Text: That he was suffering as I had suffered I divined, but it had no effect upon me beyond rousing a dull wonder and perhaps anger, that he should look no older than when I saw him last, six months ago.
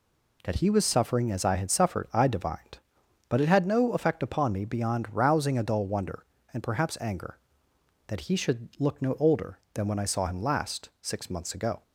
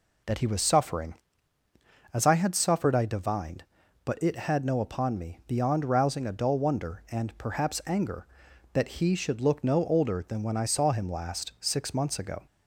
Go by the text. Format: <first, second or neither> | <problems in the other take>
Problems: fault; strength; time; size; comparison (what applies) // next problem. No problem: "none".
first | skips "effect"; at 4.8 s